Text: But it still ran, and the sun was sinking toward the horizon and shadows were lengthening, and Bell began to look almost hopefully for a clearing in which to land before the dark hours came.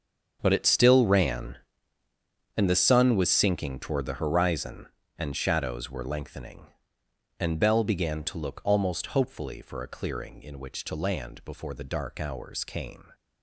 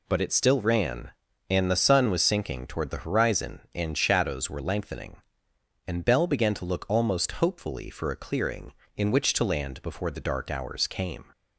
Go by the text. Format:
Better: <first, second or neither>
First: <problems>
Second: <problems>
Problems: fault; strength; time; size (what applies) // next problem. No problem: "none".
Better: second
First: gets quieter; strong; throughout; 15 dB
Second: none